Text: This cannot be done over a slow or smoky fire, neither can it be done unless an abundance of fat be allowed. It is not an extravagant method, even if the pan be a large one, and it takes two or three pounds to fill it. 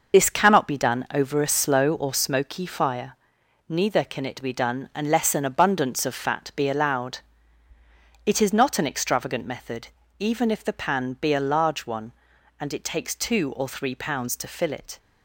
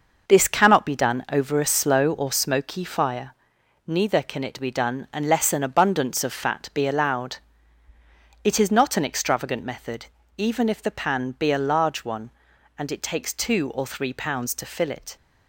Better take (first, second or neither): second